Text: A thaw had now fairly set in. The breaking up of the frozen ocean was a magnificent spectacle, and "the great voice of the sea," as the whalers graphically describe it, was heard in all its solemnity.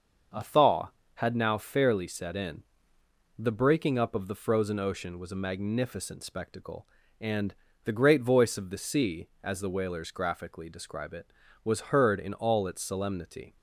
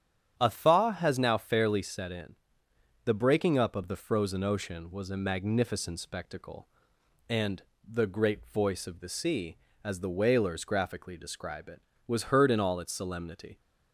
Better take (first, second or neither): first